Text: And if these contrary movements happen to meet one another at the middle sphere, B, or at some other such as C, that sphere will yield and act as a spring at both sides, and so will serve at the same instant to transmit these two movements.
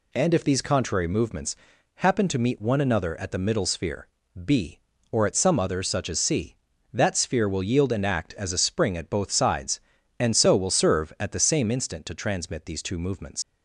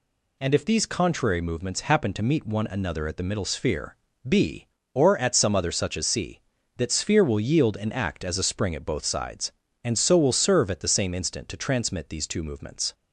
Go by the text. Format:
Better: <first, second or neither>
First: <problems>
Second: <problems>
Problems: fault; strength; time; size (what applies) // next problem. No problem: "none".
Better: second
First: pauses between "movements" and "happen"; at 1.5 s; 0.40 s long // leaves "movements" unfinished; at 13.4 s; 95 ms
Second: none